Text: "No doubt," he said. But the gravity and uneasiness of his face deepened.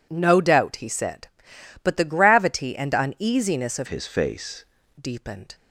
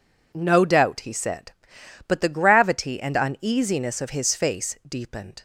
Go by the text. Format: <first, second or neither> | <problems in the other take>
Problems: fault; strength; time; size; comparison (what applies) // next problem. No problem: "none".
second | changes voice from "his" to "face"; from 3.8 to 4.6 s; 0.8 s long